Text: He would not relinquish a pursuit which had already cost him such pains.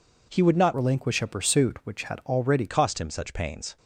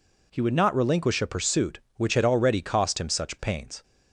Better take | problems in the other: second | changes voice from "relinquish" to "already"; from 0.7 to 2.6 s; 1.9 s long

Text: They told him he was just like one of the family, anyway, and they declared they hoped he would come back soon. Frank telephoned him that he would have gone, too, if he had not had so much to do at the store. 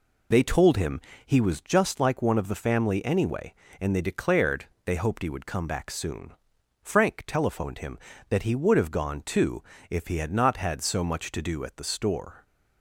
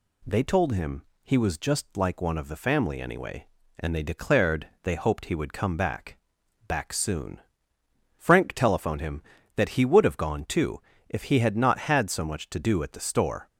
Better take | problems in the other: first | pauses between "him" and "he"; slight; at 1.0 s; 0.20 s long; slight in the first // pauses between "declared" and "they"; slight; at 4.6 s; 0.16 s long; slight in the first // says "back" twice; at 6.6 s

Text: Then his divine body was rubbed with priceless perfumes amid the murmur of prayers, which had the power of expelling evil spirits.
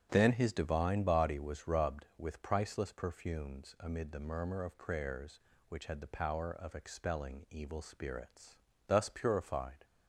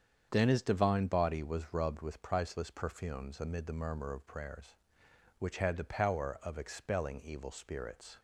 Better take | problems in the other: second | starts louder than the rest; strong; until 1.1 s; 10.5 dB; strong in the second // goes on to say "Thus purified"; noticeable; from 8.8 s on; 0.96 s long

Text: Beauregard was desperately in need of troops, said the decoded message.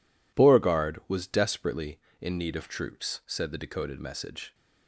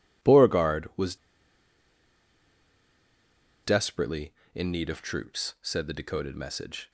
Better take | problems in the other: first | pauses between "was" and "desperately"; strong; at 1.1 s; 2.4 s long

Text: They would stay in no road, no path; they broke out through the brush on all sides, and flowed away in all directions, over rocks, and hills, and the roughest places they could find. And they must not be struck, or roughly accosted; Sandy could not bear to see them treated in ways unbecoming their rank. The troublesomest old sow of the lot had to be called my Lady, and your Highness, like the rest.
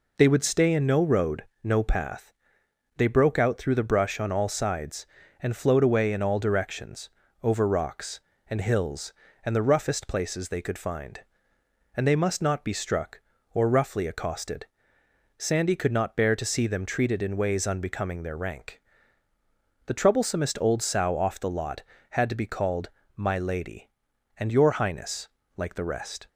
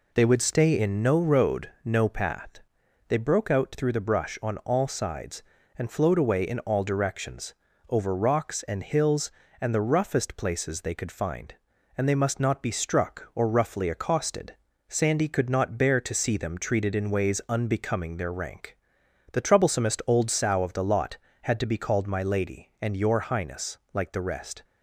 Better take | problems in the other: second | says "off" for "of"; at 21.1 s // pauses between "called" and "my"; slight; at 22.8 s; 0.26 s long

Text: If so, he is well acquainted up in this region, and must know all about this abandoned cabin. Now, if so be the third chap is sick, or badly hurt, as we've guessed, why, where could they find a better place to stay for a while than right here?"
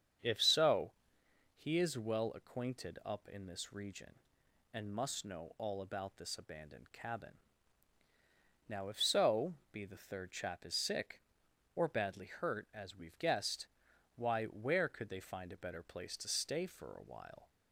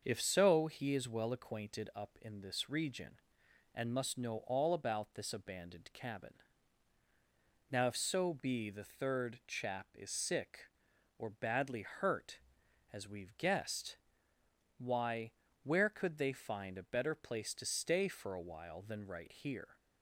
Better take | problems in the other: second | starts louder than the rest; strong; until 1.8 s; 7.5 dB; also in the second // pauses between "so" and "be"; slight; at 9.5 s; 0.18 s long // stops before "than right here"; at 17.4 s

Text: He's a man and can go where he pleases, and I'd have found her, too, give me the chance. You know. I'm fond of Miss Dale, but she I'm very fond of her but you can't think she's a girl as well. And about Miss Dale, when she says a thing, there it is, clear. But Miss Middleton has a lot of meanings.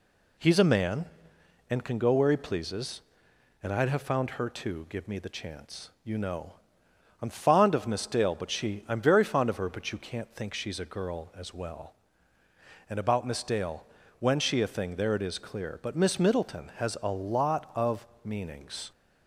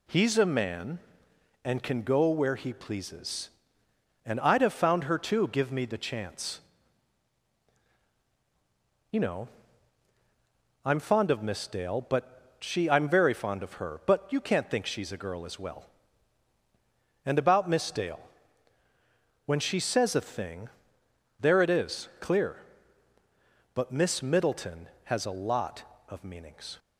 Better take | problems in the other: second | skips "says"; at 14.6 s // pauses between "of" and "meanings"; slight; at 18.0 s; 0.18 s long

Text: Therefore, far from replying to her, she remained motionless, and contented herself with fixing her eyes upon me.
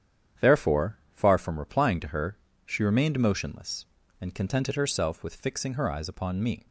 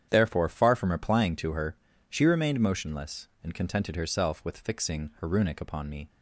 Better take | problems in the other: first | starts louder than the rest; strong; until 1.1 s; 9 dB; strong in the first // says "runic" for "eyes"; at 5.2 s

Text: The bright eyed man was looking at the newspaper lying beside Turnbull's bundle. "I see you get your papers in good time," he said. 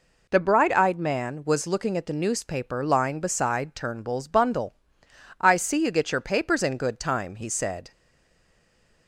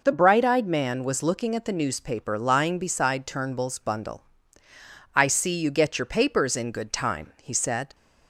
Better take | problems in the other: second | stays silent after the last word; noticeable; from 7.9 s on; 1.1 s long

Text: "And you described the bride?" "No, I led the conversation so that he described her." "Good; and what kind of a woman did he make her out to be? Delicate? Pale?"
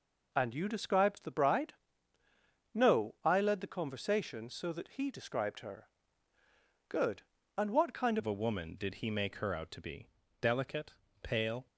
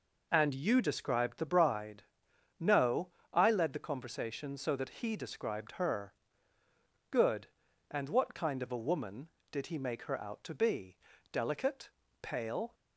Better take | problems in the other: second | changes voice at "of"; from 8.1 s on; 3.5 s long

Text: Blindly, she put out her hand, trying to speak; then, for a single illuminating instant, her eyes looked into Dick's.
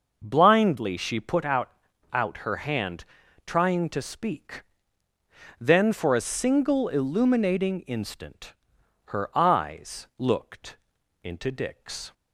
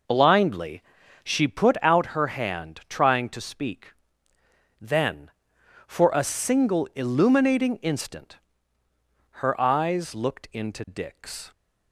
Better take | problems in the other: second | says "out" twice; at 2.1 s // pauses between "looked" and "into"; noticeable; at 10.7 s; 0.46 s long

